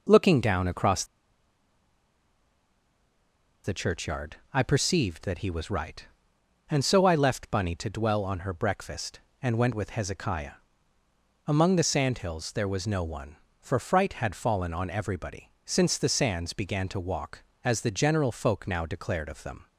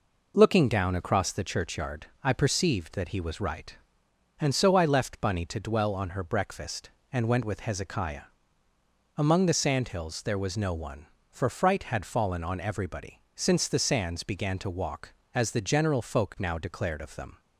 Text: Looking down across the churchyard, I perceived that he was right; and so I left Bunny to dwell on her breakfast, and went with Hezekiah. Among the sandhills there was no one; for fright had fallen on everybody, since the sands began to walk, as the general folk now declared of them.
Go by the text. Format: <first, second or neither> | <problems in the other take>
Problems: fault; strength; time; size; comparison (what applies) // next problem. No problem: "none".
second | pauses between "across" and "the"; strong; at 1.0 s; 2.6 s long